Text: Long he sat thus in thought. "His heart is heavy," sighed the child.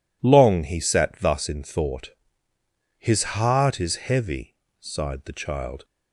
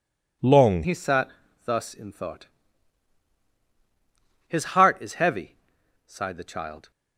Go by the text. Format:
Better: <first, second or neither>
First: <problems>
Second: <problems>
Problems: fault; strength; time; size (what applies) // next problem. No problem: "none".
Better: first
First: none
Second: changes voice at "he"; from 0.8 s on; 6.1 s long // pauses between "sat" and "thus"; slight; at 1.3 s; 0.34 s long